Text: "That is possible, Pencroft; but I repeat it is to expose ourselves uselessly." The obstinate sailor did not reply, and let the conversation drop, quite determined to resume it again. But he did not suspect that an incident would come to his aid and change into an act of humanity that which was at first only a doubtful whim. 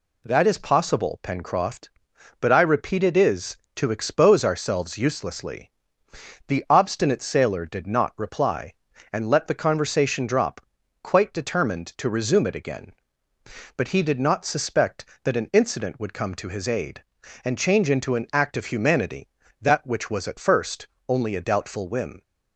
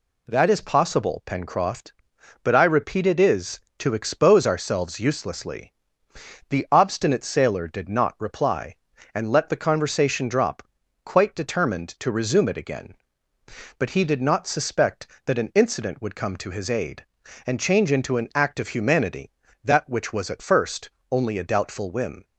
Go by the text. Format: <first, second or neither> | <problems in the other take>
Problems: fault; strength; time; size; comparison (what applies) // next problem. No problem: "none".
neither | pauses between "first" and "only"; slight; the same in both